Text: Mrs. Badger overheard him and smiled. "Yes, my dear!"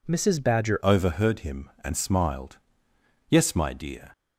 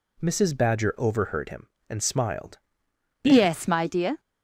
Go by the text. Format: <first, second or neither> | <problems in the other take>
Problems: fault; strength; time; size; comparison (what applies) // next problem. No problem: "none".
second | changes voice at "overheard"; from 0.8 s on; 3.3 s long